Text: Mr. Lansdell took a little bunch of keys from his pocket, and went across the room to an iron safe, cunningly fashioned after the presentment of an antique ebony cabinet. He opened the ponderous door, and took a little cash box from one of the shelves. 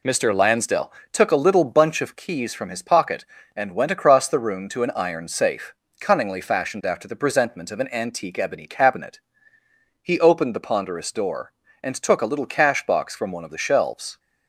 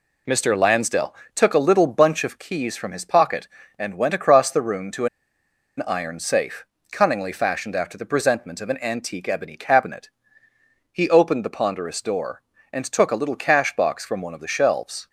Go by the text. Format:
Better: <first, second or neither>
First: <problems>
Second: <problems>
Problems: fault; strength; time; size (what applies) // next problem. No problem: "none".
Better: first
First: pauses between "Lansdell" and "took"; slight; at 0.9 s; 0.22 s long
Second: pauses between "Lansdell" and "took"; slight; at 1.1 s; 0.22 s long // pauses between "to" and "an"; noticeable; at 5.0 s; 0.71 s long